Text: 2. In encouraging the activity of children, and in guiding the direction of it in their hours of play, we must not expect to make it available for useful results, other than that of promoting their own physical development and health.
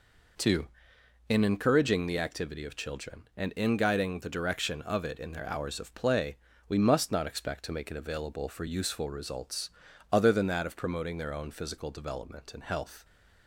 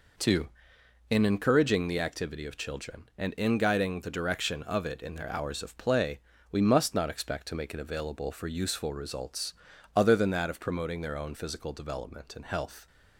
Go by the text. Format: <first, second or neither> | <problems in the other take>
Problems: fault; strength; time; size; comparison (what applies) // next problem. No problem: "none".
neither | none